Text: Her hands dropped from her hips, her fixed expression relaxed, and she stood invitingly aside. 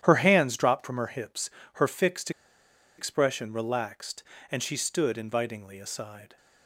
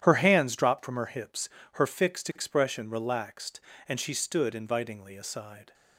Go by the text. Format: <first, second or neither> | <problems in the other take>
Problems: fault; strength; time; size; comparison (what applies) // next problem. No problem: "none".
second | starts louder than the rest; strong; until 1.0 s; 10.5 dB; strong in the second // pauses between "fixed" and "expression"; noticeable; at 2.3 s; 0.66 s long